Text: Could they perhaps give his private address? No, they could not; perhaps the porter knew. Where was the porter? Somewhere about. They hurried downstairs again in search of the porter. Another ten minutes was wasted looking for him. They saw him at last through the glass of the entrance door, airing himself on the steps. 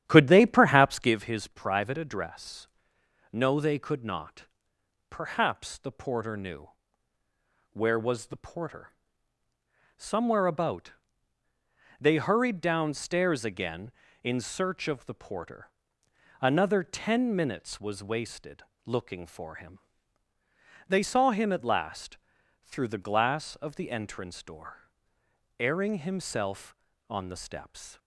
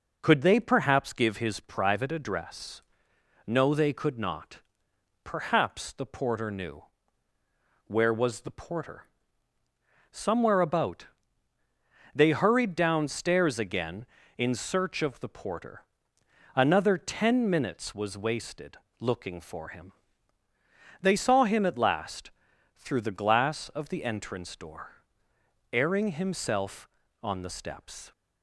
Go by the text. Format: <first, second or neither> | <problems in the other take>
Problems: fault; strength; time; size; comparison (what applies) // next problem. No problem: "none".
second | starts louder than the rest; strong; until 1.1 s; 10.5 dB // pauses between "wasted" and "looking"; slight; at 18.6 s; 0.22 s long; slight in the second // pauses between "last" and "through"; at 22.1 s; 0.44 s long; also in the second